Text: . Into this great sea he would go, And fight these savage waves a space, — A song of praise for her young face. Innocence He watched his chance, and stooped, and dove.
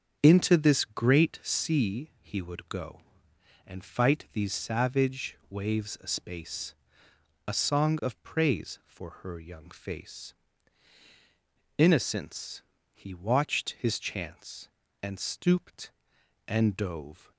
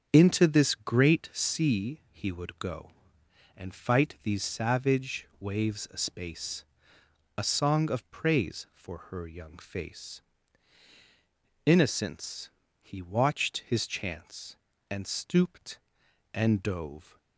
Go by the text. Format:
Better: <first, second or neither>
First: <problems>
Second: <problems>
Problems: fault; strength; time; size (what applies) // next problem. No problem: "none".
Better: neither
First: starts louder than the rest; until 1.2 s; 6.5 dB // pauses between "Innocence" and "He"; slight; at 12.6 s; 0.32 s long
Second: starts louder than the rest; until 1.1 s; 6.5 dB // pauses between "Innocence" and "He"; slight; at 12.4 s; 0.32 s long